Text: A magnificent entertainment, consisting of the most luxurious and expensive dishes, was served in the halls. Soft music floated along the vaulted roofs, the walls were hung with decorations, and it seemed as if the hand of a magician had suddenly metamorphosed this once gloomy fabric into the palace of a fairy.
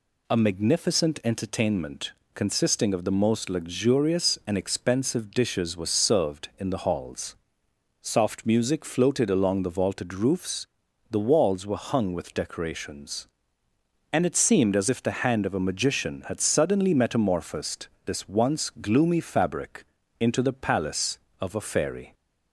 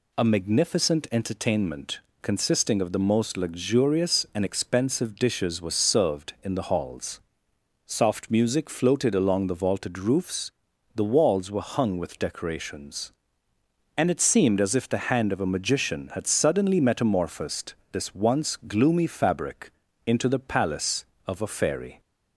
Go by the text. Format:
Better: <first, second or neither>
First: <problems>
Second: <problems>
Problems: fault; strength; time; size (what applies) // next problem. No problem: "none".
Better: neither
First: pauses between "metamorphosed" and "this"; slight; at 17.8 s; 0.18 s long // pauses between "fabric" and "into"; at 19.8 s; 0.38 s long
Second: pauses between "metamorphosed" and "this"; slight; at 17.7 s; 0.18 s long // pauses between "fabric" and "into"; at 19.6 s; 0.38 s long